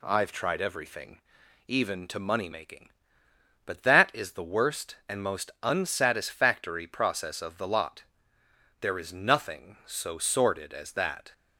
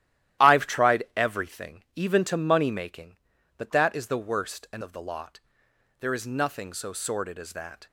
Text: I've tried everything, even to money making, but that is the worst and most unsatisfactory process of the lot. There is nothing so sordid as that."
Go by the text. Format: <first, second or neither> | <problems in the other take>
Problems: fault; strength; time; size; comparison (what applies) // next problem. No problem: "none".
first | starts louder than the rest; strong; until 1.5 s; 13 dB // skips "most unsatisfactory process"; at 4.8 s